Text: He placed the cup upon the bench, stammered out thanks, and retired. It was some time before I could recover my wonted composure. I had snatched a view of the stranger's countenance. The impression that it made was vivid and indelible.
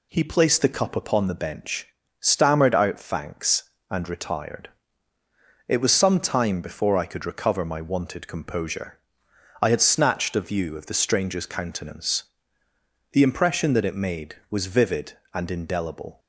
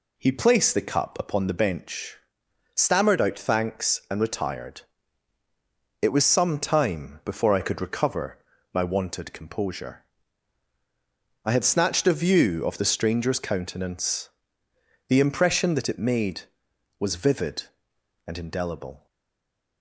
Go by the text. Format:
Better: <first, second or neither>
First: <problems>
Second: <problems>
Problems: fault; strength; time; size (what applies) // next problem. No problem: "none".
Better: first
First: none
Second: pauses between "recover" and "my"; slight; at 8.3 s; 0.34 s long // stays silent after the last word; slight; from 19.0 s on; 0.8 s long